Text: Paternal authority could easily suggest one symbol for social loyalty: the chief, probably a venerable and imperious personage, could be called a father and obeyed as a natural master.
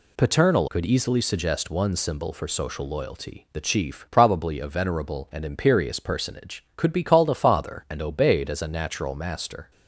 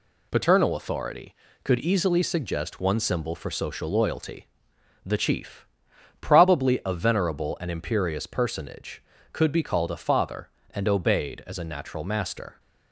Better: second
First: skips "authority"; at 0.6 s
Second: none

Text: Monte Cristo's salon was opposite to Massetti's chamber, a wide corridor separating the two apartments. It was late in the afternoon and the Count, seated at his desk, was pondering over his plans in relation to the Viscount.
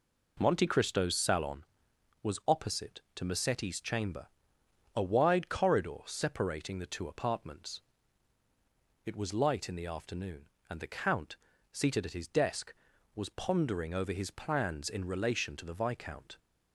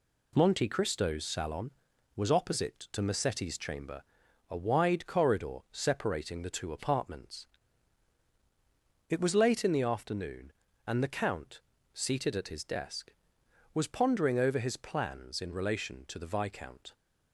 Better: second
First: says "light" for "late"; at 9.3 s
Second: none

